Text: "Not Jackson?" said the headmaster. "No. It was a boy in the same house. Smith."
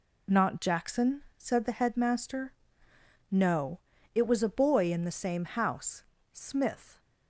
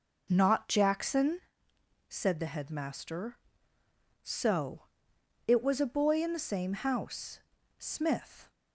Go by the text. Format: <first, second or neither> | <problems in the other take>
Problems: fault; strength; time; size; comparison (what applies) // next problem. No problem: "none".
first | says "So" for "No"; at 4.2 s